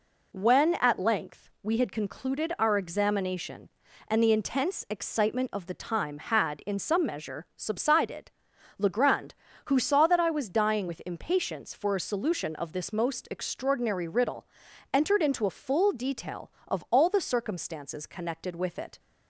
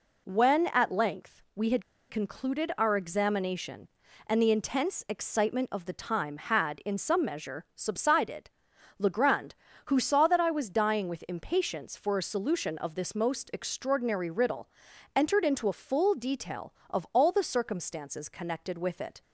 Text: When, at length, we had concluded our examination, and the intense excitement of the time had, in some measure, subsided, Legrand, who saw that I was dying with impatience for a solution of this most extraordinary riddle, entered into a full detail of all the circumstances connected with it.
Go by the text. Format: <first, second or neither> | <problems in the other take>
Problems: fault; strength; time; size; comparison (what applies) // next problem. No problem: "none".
first | pauses between "had" and "concluded"; slight; at 1.8 s; 0.28 s long